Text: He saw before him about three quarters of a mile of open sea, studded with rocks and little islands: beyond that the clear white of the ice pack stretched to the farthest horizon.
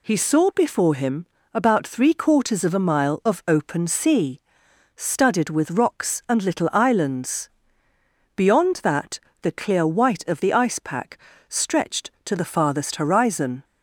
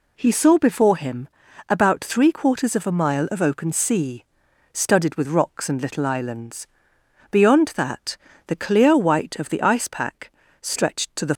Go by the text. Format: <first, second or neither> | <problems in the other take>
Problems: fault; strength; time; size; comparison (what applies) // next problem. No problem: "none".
first | pauses between "him" and "about"; at 1.2 s; 0.42 s long; slight in the first // pauses between "that" and "the"; slight; at 8.1 s; 0.30 s long; slight in the first // pauses between "pack" and "stretched"; slight; at 10.3 s; 0.30 s long; slight in the first // stops before "farthest horizon"; at 11.3 s